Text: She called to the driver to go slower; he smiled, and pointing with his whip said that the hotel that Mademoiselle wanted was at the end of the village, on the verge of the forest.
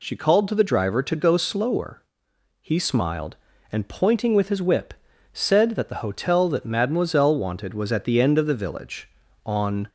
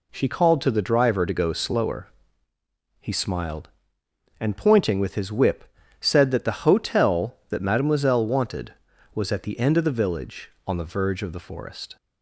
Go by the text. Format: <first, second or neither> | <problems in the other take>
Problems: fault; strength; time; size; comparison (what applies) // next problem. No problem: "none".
second | pauses between "whip" and "said"; at 4.9 s; 0.38 s long; slight in the second // stops before "the verge of the forest"; at 9.8 s